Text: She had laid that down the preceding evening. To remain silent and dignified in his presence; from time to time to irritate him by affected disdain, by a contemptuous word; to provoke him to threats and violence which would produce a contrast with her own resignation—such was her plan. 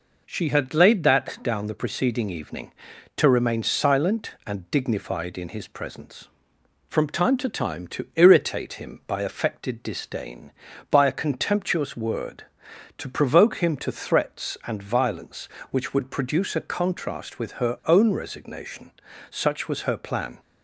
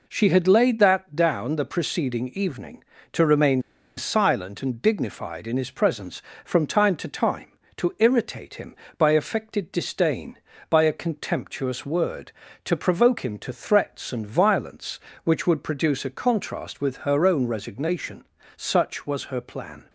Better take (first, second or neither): first